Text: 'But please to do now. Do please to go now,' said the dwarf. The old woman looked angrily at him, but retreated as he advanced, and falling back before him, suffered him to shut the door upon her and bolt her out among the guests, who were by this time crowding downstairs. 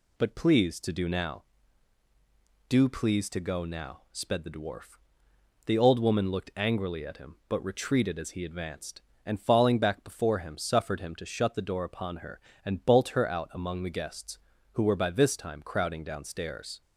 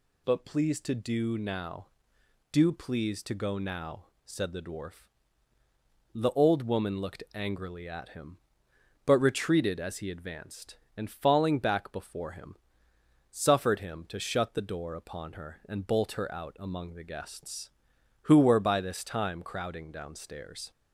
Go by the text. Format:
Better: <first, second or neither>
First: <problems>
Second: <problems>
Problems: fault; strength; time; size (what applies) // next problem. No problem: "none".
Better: second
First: says "sped" for "said"; at 4.1 s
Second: none